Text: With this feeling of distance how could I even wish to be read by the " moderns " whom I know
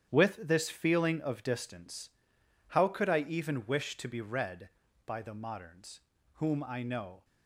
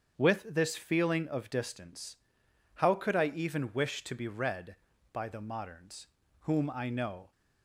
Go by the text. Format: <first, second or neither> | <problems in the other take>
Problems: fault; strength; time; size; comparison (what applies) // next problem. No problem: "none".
second | gets quieter; strong; throughout; 12.5 dB // starts louder than the rest; strong; until 1.1 s; 10 dB; strong in the second // pauses between "distance" and "how"; noticeable; at 2.0 s; 0.60 s long; noticeable in the second